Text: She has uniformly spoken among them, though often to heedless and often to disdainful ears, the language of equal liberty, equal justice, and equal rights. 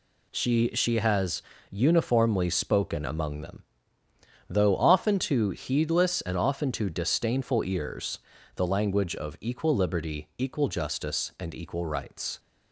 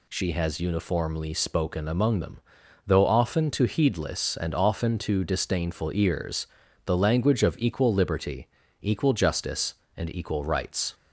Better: second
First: says "She" twice; at 0.7 s // pauses between "has" and "uniformly"; slight; at 1.4 s; 0.30 s long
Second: none

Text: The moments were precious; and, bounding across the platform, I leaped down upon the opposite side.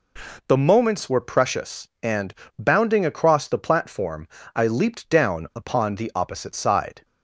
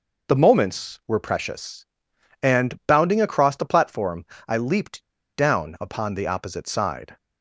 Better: first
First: none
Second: pauses between "leaped" and "down"; slight; at 5.0 s; 0.30 s long

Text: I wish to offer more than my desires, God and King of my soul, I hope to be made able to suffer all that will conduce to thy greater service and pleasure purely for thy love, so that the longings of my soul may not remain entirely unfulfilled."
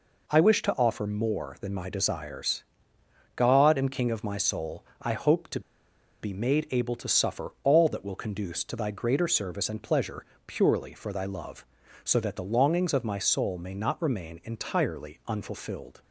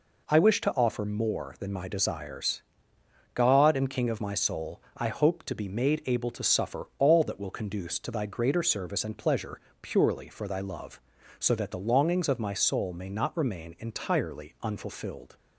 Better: second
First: pauses between "to" and "be"; noticeable; at 5.5 s; 0.62 s long // pauses between "pleasure" and "purely"; slight; at 10.2 s; 0.22 s long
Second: pauses between "pleasure" and "purely"; slight; at 9.5 s; 0.22 s long

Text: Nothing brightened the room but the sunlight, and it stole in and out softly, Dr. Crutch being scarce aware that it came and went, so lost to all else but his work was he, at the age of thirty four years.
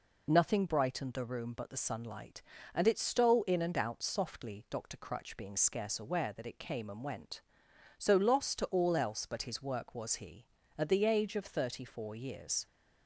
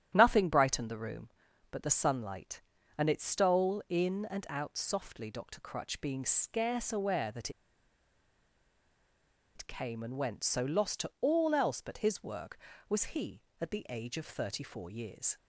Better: first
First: none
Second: starts louder than the rest; strong; until 1.1 s; 10.5 dB // pauses between "that" and "it"; strong; at 7.4 s; 2.0 s long

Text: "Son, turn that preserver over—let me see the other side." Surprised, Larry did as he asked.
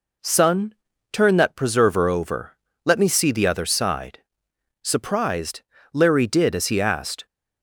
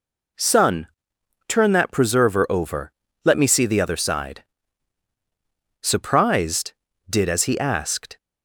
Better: first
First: none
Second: skips "Larry"; at 6.9 s

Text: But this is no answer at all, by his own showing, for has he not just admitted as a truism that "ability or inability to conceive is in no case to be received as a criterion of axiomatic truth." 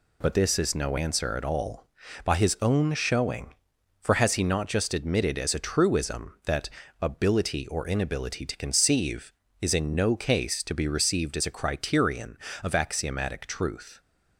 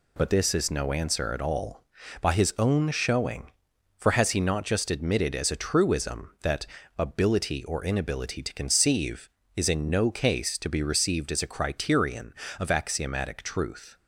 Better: neither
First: pauses between "that" and "ability"; slight; at 6.6 s; 0.32 s long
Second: pauses between "that" and "ability"; slight; at 6.6 s; 0.32 s long

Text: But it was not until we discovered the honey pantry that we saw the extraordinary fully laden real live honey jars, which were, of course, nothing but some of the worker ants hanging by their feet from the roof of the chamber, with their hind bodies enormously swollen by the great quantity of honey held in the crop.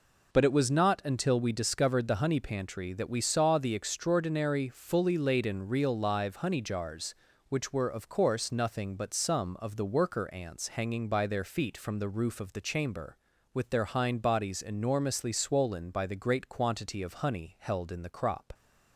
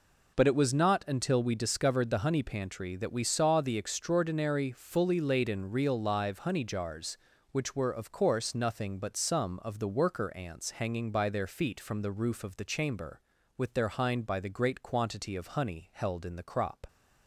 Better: first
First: none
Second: skips "bodies enormously swollen"; at 14.2 s

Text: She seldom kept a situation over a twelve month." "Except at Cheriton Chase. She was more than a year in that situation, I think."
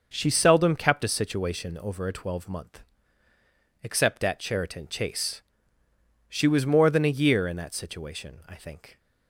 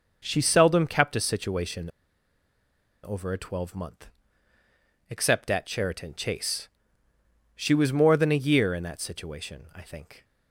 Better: first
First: starts louder than the rest; noticeable; until 1.1 s; 6 dB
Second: starts louder than the rest; noticeable; until 1.2 s; 6 dB // pauses between "situation" and "over"; at 1.8 s; 1.1 s long

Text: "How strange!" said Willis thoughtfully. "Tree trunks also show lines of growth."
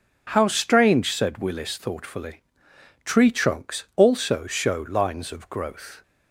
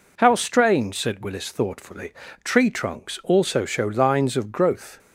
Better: neither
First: none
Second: none

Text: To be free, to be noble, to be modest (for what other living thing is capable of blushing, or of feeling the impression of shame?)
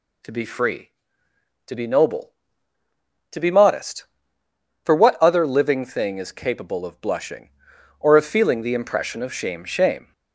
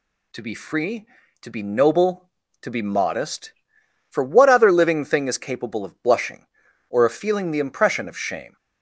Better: second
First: says "shame" twice; at 9.6 s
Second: none

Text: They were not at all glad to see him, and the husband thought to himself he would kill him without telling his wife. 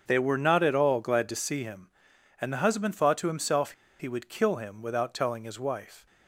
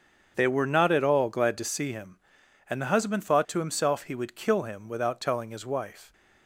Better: second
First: starts louder than the rest; strong; until 1.0 s; 7.5 dB // pauses between "himself" and "he"; slight; at 3.7 s; 0.26 s long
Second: starts louder than the rest; strong; until 1.3 s; 7.5 dB

